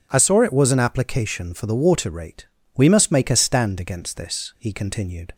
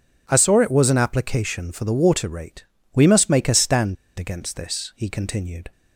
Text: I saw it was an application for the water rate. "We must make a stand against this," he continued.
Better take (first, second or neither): first